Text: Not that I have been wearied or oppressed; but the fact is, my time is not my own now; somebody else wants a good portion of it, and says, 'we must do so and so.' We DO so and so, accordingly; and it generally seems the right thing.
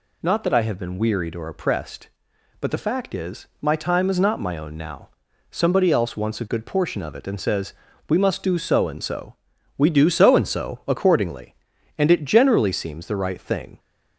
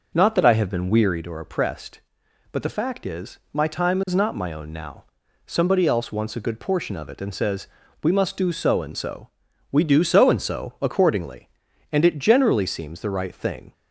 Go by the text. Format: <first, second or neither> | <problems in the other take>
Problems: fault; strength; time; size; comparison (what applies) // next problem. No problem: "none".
first | starts louder than the rest; noticeable; until 1.2 s; 5.5 dB